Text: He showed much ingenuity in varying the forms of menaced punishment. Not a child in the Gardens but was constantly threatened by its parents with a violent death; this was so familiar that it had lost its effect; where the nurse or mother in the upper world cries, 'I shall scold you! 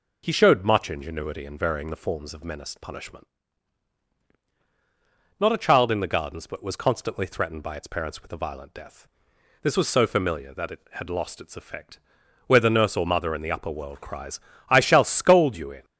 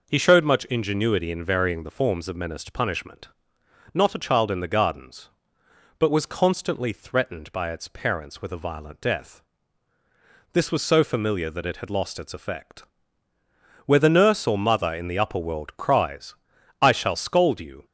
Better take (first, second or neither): second